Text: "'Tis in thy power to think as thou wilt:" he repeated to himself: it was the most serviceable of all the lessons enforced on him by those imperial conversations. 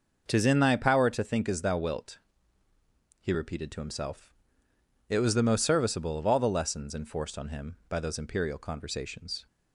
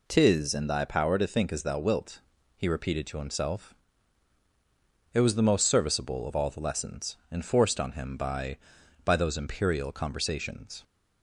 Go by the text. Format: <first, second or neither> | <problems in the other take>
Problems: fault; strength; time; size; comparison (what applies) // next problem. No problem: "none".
first | says "by" twice; at 9.0 s